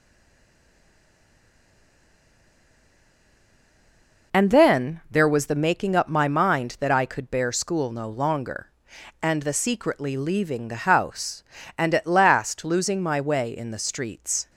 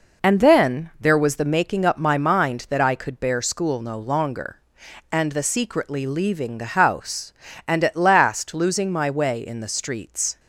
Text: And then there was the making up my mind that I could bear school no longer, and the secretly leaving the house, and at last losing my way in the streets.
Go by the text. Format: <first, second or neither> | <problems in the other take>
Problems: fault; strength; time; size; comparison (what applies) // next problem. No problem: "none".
second | stays silent before the first word; strong; until 4.3 s; 4.3 s long